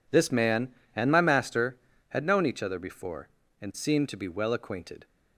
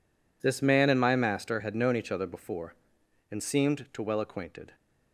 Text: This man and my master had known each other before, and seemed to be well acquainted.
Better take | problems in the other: first | skips "be"; at 4.0 s

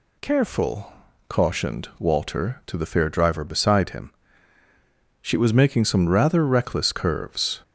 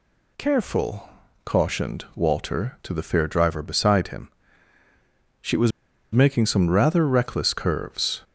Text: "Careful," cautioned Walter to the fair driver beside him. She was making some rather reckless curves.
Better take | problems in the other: first | pauses between "was" and "making"; at 5.7 s; 0.43 s long

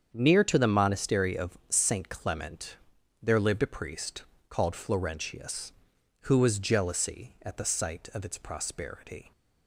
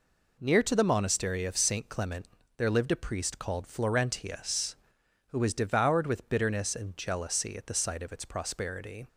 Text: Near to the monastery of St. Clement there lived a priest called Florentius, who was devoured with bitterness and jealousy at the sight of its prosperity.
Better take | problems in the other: second | starts louder than the rest; strong; until 1.1 s; 7.5 dB // pauses between "Clement" and "there"; at 2.7 s; 0.44 s long; slight in the second // pauses between "priest" and "called"; slight; at 4.2 s; 0.26 s long // skips "devoured with bitterness and"; at 6.5 s

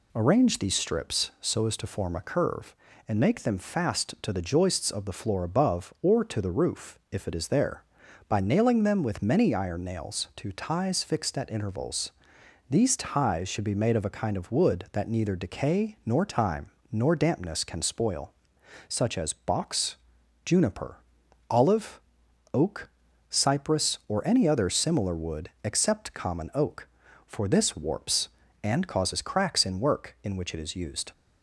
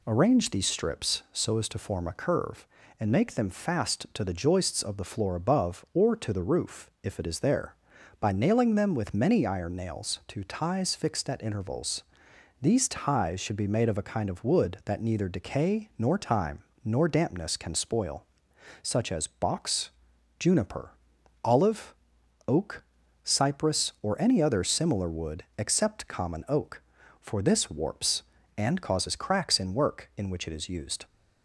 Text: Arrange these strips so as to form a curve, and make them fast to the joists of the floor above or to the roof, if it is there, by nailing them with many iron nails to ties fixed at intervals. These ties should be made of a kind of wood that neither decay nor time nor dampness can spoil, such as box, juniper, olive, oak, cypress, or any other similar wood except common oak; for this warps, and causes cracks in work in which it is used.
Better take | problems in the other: neither | pauses between "time" and "nor"; slight; the same in both // pauses between "wood" and "except"; slight; the same in both

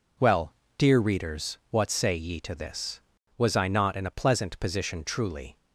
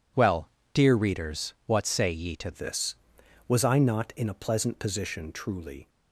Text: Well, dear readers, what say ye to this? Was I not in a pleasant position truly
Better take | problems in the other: first | changes voice at "this"; from 2.5 s on; 3.3 s long

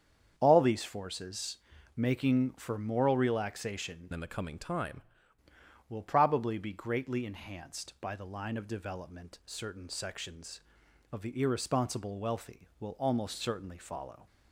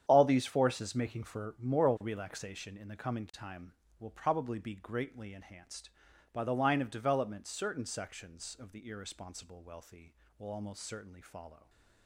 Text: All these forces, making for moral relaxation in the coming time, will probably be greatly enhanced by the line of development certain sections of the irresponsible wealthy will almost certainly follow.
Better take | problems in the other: second | starts louder than the rest; strong; until 1.3 s; 8 dB; strong in the second // changes voice from "in" to "time"; from 4.1 to 5.0 s; 0.9 s long

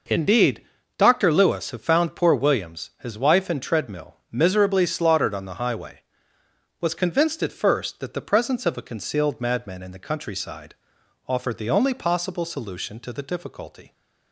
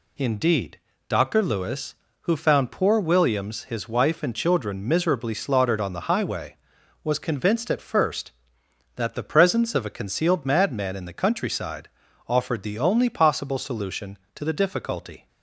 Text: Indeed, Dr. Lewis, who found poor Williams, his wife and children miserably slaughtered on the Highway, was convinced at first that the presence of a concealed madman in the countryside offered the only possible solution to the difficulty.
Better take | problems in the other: second | says "treadmill" for "children"; at 3.6 s // pauses between "countryside" and "offered"; noticeable; at 10.7 s; 0.52 s long; also in the second

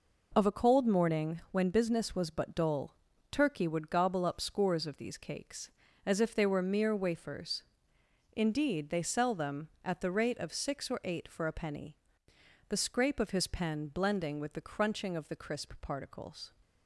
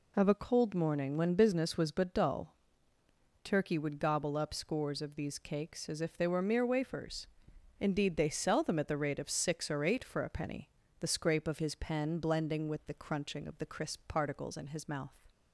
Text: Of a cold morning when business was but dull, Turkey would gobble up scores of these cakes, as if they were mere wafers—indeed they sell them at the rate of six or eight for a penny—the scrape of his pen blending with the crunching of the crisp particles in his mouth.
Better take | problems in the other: second | stops before "in his mouth"; at 16.6 s

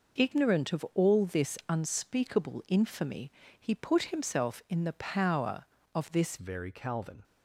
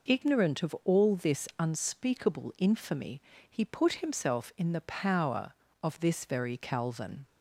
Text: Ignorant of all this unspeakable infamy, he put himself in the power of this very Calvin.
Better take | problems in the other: second | changes voice at "very"; from 6.3 s on; 0.9 s long

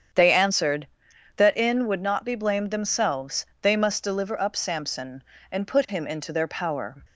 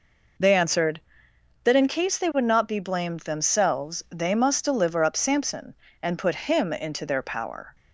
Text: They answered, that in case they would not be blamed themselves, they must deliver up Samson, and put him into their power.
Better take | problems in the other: second | starts louder than the rest; strong; until 1.6 s; 8 dB // skips "case they"; at 1.8 s

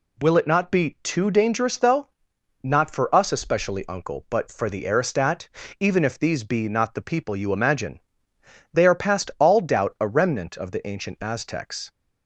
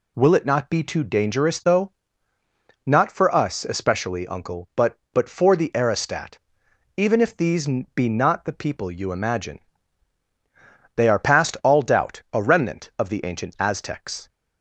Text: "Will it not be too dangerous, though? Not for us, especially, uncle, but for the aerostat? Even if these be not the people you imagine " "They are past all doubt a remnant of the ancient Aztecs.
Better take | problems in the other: first | says "but" twice; at 5.1 s // pauses between "these" and "be"; slight; at 7.6 s; 0.30 s long

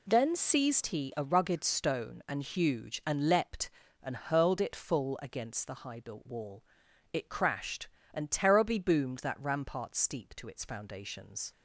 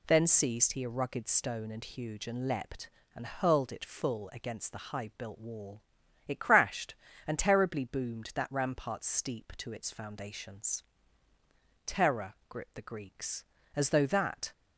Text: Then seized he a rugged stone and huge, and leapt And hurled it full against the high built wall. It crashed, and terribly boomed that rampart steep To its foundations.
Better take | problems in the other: first | goes on to say "Terror gripped the Greeks As though that"; strong; from 11.8 s on; 2.6 s long

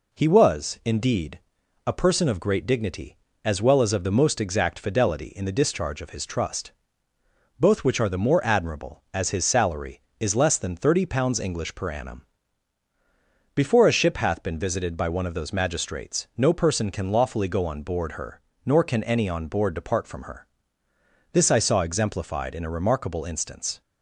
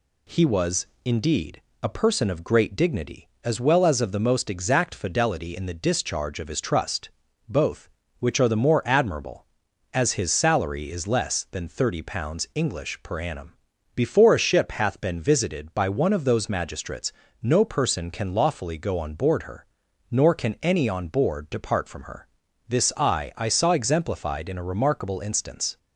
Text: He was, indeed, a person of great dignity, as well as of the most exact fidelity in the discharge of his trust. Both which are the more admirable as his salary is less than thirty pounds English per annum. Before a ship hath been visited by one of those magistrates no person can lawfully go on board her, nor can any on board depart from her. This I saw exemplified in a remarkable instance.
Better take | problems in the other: first | pauses between "magistrates" and "no"; slight; at 17.1 s; 0.30 s long // says "I" twice; at 23.3 s

